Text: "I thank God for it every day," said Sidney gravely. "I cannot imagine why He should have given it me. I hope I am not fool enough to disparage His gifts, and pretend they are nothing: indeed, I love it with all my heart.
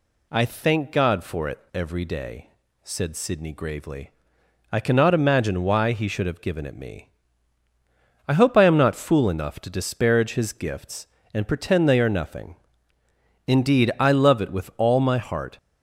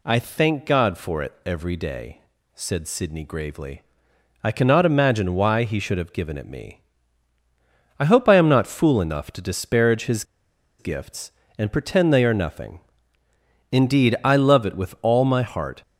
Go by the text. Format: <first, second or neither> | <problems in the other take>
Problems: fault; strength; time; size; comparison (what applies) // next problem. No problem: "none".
first | pauses between "His" and "gifts"; noticeable; at 10.2 s; 0.54 s long